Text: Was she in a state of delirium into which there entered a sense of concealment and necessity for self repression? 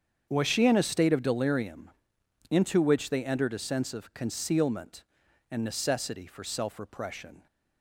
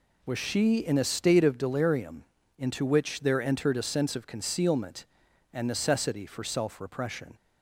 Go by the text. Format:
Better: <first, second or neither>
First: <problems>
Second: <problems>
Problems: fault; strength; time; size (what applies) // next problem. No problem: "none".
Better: second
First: starts louder than the rest; strong; until 1.3 s; 7.5 dB // pauses between "delirium" and "into"; noticeable; at 1.8 s; 0.60 s long // says "they" for "there"; at 3.0 s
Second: pauses between "delirium" and "into"; slight; at 2.2 s; 0.34 s long